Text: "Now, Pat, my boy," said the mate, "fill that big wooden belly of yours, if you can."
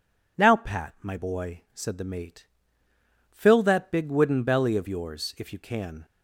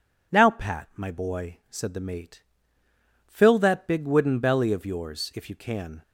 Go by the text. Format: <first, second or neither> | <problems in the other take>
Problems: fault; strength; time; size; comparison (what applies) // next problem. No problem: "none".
neither | none